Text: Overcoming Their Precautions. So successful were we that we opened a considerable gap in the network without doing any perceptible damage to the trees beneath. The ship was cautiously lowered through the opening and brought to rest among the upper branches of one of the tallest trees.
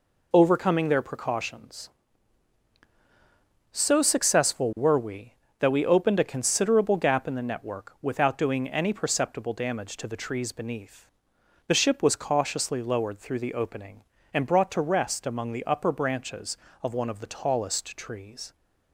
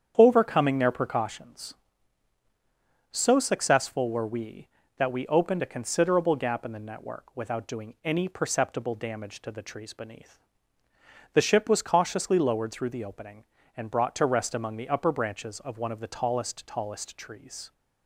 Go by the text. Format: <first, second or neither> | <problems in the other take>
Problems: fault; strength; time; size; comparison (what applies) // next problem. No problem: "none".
first | starts louder than the rest; strong; until 1.1 s; 8 dB // says "tallest" twice; at 16.6 s